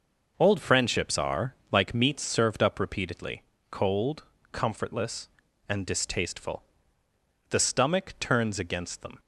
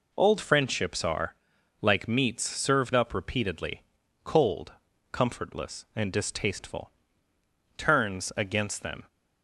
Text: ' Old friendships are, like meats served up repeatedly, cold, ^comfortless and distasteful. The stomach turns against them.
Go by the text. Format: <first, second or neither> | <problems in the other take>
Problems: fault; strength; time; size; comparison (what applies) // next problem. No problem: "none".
first | skips "The stomach"; at 7.3 s